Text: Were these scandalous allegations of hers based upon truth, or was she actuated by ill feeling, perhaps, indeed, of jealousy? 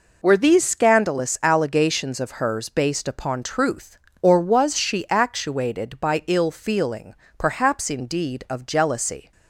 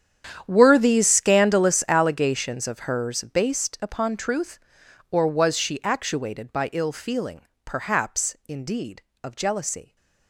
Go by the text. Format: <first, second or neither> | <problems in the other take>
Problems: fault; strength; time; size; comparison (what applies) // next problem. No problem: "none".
first | gets quieter; strong; throughout; 17 dB